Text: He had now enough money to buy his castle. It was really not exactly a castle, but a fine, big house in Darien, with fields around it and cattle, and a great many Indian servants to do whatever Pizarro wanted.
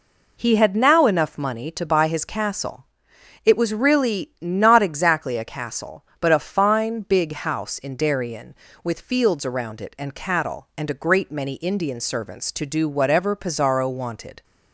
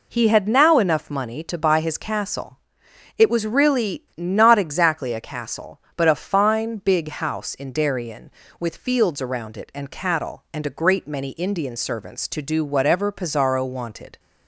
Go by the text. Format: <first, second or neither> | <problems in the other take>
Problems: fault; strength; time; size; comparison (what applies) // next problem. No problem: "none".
neither | none